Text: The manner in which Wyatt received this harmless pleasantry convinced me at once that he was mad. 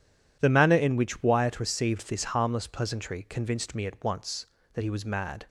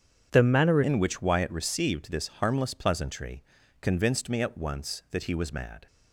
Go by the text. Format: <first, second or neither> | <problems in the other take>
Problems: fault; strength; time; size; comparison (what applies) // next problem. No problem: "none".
first | starts louder than the rest; strong; until 1.3 s; 8 dB // changes voice at "in"; from 0.8 s on; 5.0 s long // pauses between "pleasantry" and "convinced"; at 3.4 s; 0.38 s long